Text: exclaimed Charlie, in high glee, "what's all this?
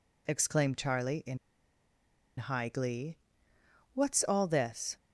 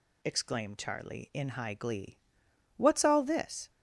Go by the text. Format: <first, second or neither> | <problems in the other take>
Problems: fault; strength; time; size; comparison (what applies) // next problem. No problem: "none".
second | pauses between "in" and "high"; at 1.3 s; 1.0 s long